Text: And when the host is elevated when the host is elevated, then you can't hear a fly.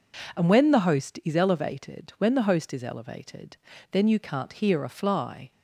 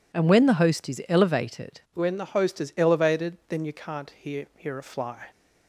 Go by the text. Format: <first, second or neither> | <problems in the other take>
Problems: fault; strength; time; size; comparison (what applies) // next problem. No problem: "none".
first | says "hear" twice; at 4.5 s